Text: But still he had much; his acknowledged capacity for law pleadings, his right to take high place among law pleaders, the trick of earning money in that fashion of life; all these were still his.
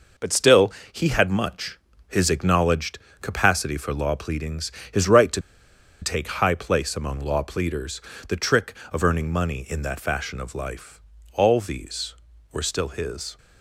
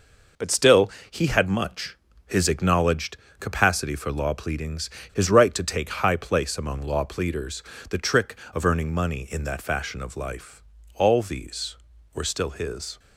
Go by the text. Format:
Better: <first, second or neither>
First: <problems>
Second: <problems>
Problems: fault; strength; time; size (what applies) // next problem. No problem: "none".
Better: second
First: pauses between "still" and "he"; slight; at 0.7 s; 0.20 s long // pauses between "acknowledged" and "capacity"; slight; at 2.9 s; 0.22 s long // pauses between "to" and "take"; noticeable; at 5.4 s; 0.61 s long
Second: pauses between "still" and "he"; slight; at 0.9 s; 0.20 s long // pauses between "acknowledged" and "capacity"; slight; at 3.1 s; 0.22 s long